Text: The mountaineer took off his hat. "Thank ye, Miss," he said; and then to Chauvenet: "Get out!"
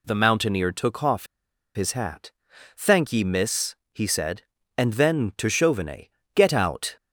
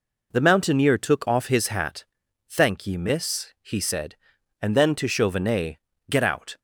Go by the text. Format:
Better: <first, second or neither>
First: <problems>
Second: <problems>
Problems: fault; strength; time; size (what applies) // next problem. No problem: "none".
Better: second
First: pauses between "off" and "his"; noticeable; at 1.2 s; 0.49 s long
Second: none